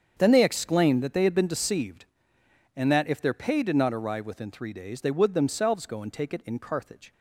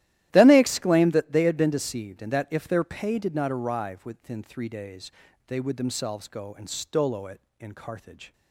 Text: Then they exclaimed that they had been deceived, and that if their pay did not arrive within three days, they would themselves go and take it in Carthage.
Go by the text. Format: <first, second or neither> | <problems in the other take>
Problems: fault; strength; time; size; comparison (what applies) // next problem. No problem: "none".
first | starts louder than the rest; strong; until 1.3 s; 14 dB; strong in the first // says "stolo" for "take"; at 6.6 s